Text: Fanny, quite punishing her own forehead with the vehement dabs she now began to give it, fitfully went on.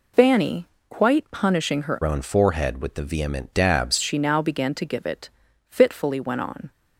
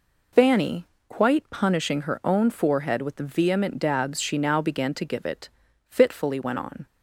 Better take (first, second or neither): second